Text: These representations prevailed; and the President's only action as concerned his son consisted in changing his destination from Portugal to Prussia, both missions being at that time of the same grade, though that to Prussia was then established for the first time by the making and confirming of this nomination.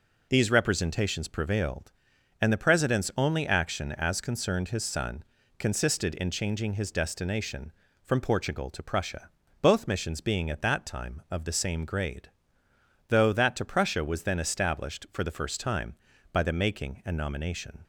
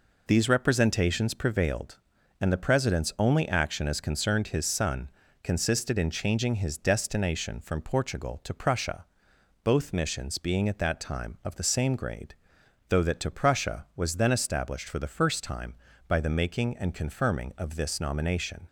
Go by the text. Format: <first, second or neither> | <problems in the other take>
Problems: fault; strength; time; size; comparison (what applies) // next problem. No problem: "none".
second | pauses between "son" and "consisted"; slight; at 5.2 s; 0.36 s long; slight in the second // skips "confirming of this"; at 17.1 s